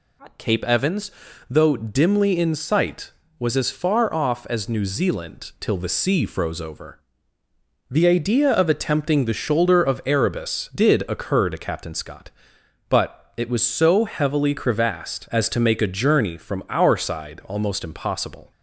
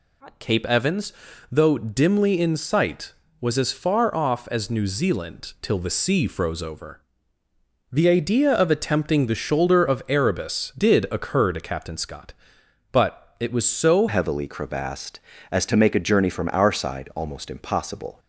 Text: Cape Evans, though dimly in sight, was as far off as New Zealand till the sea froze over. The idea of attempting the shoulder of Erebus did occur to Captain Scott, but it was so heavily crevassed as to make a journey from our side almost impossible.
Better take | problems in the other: first | changes voice at "heavily"; from 14.0 s on; 4.1 s long

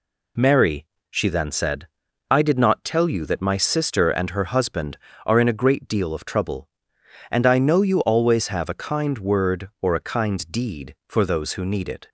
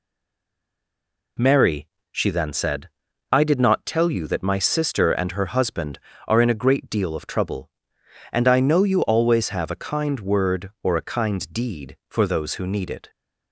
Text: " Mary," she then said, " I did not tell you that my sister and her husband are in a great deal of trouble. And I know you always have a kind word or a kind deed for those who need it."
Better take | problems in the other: first | stays silent before the first word; noticeable; until 1.3 s; 1.3 s long

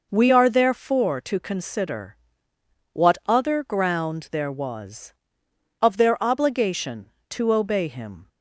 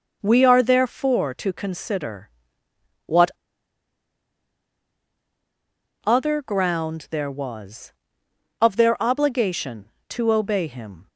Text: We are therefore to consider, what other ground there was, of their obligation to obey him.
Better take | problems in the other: first | pauses between "what" and "other"; strong; at 3.2 s; 2.7 s long

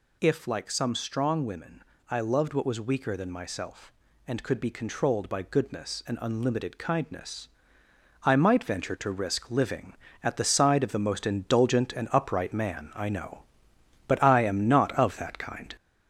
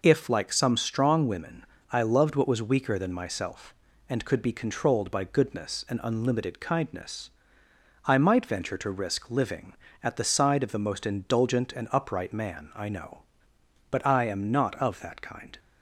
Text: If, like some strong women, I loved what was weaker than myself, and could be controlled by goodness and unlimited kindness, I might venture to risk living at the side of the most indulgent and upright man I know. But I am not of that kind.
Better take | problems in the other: second | gets louder; noticeable; throughout; 4.5 dB

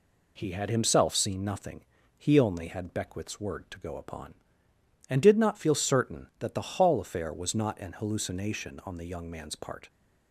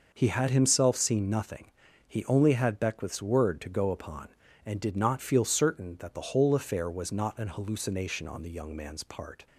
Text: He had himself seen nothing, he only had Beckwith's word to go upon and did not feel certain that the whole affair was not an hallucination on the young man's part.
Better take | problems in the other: second | says "hall" for "whole"; at 6.7 s

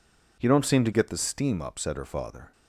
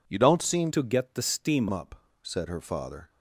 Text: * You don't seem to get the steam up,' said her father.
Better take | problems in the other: first | changes voice from "to" to "steam"; from 0.7 to 1.6 s; 0.9 s long

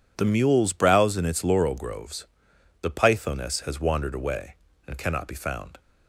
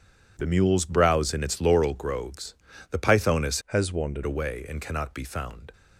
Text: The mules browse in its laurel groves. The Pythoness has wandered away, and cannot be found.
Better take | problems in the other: first | changes voice from "has" to "wandered"; from 3.6 to 4.2 s; 0.6 s long

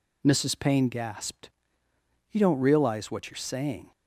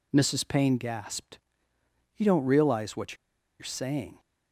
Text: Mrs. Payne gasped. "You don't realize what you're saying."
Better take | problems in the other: first | pauses between "what" and "you're"; at 3.1 s; 0.44 s long

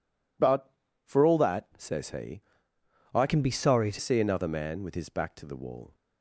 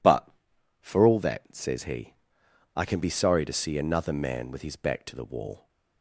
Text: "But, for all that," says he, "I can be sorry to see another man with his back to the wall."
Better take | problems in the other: second | changes voice from "can" to "to"; from 3.2 to 3.9 s; 0.7 s long

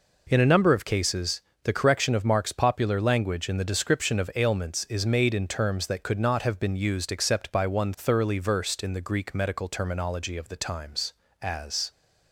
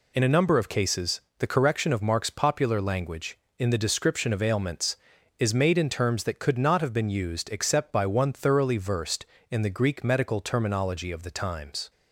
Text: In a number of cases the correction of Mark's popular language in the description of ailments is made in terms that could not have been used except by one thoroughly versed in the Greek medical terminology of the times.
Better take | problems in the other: second | pauses between "cases" and "the"; slight; at 1.3 s; 0.24 s long; slight in the second // goes on to say "As"; slight; from 11.4 s on; 0.48 s long

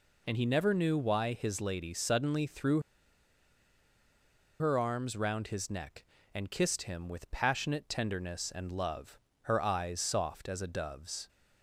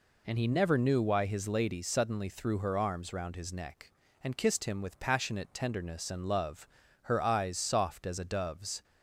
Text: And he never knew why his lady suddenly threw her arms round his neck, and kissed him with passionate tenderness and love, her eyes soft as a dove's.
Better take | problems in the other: second | pauses between "threw" and "her"; strong; at 2.7 s; 1.7 s long

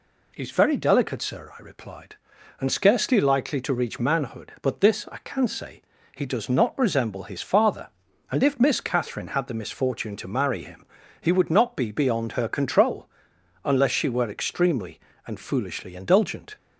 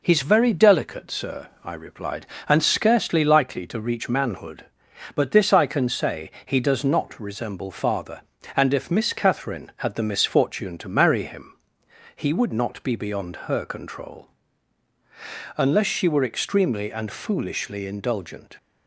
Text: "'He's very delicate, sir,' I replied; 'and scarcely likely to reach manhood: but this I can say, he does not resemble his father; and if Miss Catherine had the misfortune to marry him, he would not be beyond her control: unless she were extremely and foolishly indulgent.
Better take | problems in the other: first | skips "his"; at 7.7 s

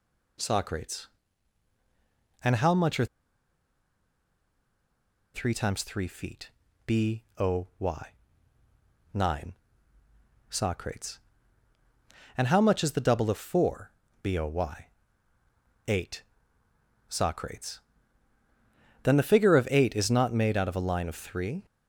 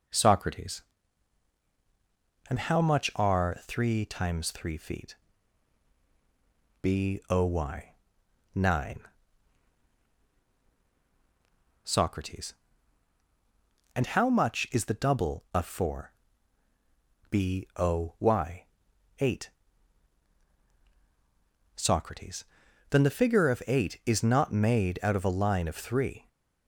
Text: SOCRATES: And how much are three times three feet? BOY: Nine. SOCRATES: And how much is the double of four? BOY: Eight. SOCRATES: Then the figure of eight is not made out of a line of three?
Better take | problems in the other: second | pauses between "are" and "three"; strong; at 3.0 s; 2.2 s long

